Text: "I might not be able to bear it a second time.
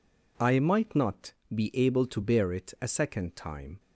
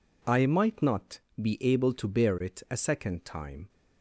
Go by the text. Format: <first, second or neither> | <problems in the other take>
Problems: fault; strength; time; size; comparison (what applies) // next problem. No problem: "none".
neither | pauses between "not" and "be"; slight; the same in both